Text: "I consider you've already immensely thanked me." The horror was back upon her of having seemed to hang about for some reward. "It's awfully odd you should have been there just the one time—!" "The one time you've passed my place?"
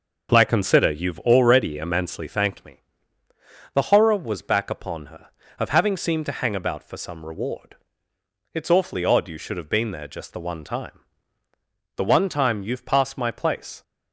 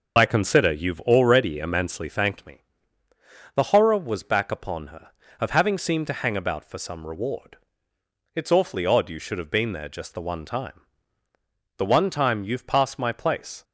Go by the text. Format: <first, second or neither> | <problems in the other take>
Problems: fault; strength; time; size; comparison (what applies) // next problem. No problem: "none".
first | loses the start of "I"; at 0.1 s; 55 ms